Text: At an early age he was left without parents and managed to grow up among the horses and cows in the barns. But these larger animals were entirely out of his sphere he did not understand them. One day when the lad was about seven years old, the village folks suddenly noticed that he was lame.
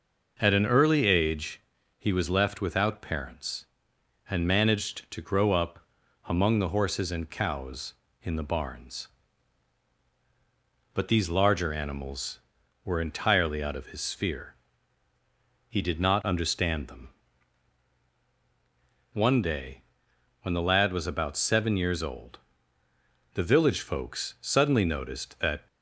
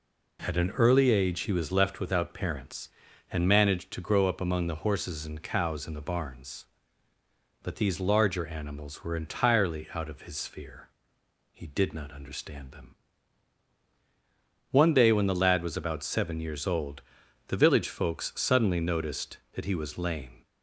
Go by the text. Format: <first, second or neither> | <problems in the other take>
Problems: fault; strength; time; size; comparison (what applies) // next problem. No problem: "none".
second | pauses between "age" and "he"; slight; at 1.6 s; 0.36 s long // pauses between "up" and "among"; noticeable; at 5.7 s; 0.46 s long // pauses between "sphere" and "he"; at 14.5 s; 1.1 s long; noticeable in the second // pauses between "day" and "when"; noticeable; at 19.8 s; 0.58 s long // stops before "he was lame"; at 25.6 s